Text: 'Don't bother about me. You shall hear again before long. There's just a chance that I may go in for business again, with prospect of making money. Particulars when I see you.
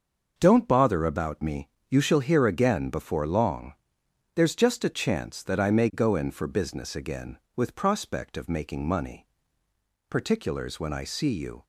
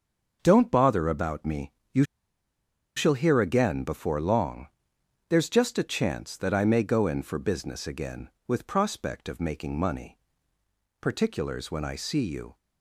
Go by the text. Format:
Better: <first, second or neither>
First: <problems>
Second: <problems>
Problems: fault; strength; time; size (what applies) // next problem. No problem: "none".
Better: first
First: starts louder than the rest; until 1.3 s; 6.5 dB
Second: starts louder than the rest; until 1.4 s; 6.5 dB // pauses between "You" and "shall"; noticeable; at 2.0 s; 0.92 s long